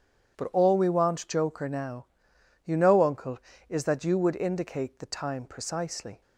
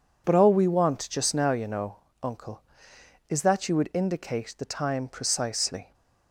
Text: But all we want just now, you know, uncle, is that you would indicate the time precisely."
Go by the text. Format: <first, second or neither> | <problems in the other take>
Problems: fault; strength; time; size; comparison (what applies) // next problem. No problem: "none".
second | says "joker" for "just"; at 1.2 s